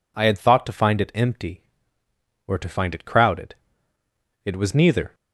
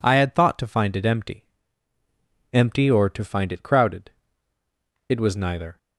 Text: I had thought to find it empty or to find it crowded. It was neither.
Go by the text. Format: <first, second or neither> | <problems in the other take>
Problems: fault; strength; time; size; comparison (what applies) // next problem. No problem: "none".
first | says "empty" twice; at 2.5 s